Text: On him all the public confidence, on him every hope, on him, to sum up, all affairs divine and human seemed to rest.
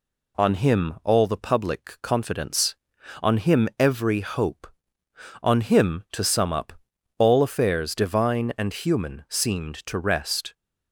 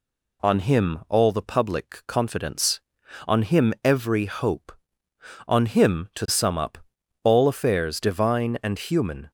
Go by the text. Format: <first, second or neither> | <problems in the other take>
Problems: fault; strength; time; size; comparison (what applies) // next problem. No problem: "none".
first | stops before "seemed to rest"; at 9.2 s